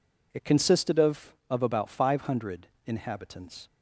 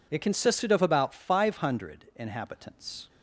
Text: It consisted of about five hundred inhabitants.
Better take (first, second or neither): second